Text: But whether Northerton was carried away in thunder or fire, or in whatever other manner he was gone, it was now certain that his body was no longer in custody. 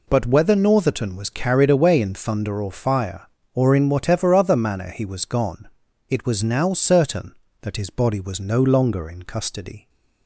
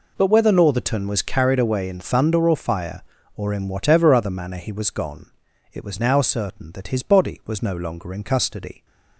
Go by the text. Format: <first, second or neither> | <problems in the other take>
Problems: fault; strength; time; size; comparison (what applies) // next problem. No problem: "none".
neither | none